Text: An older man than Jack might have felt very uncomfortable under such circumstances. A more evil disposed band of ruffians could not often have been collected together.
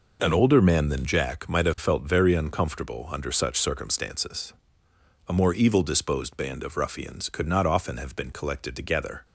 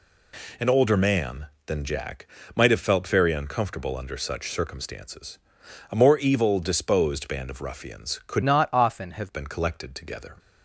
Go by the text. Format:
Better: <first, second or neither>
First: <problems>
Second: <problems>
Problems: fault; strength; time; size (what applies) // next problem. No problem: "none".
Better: first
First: none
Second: pauses between "Jack" and "might"; slight; at 2.2 s; 0.28 s long // changes voice from "not" to "have"; from 8.4 to 9.3 s; 0.9 s long